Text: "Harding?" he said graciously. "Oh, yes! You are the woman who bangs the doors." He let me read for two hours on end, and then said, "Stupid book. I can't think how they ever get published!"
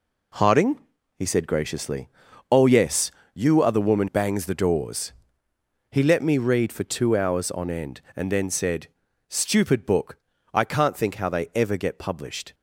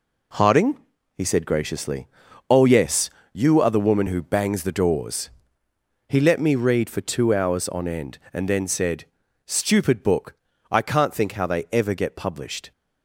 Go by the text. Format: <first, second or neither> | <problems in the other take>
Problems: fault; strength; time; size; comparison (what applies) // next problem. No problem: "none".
second | skips "who"; at 4.0 s